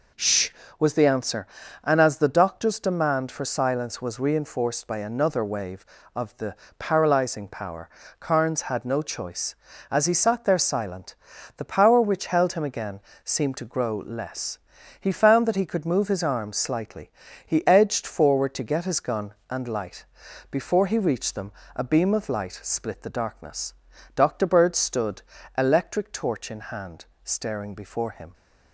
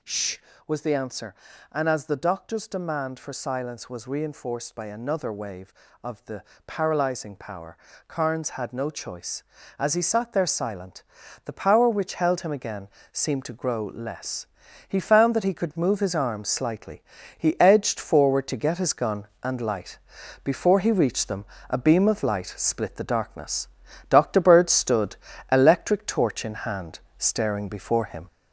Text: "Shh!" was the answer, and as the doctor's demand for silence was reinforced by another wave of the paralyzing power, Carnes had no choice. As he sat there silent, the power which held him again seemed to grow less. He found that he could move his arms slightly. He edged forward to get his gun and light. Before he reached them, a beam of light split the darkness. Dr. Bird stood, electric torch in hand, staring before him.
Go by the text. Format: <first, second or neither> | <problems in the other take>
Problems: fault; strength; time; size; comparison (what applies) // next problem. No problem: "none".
first | gets louder; noticeable; throughout; 4.5 dB // pauses between "the" and "paralyzing"; slight; at 6.4 s; 0.24 s long; slight in the first // pauses between "again" and "seemed"; slight; at 12.8 s; 0.24 s long; slight in the first